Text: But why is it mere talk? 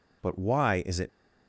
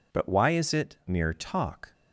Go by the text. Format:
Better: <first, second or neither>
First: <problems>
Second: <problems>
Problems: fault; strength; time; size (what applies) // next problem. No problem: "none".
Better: second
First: stops before "mere talk"; at 1.0 s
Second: none